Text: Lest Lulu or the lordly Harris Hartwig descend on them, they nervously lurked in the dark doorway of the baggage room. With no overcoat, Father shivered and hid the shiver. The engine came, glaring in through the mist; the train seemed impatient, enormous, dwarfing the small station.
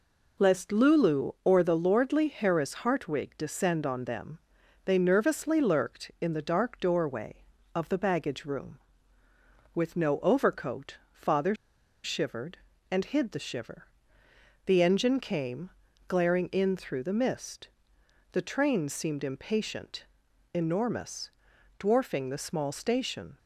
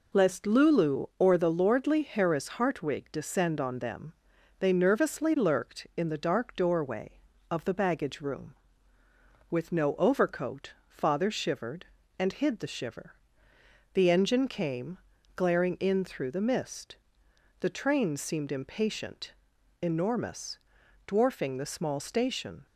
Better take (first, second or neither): second